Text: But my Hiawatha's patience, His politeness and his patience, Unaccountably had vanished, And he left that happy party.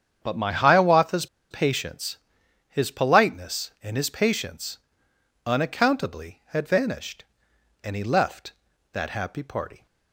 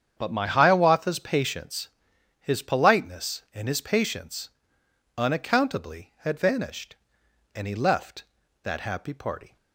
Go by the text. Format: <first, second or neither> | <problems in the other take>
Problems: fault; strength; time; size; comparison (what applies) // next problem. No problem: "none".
second | starts louder than the rest; strong; until 1.2 s; 8 dB; strong in the second // pauses between "Hiawatha's" and "patience"; slight; at 1.2 s; 0.24 s long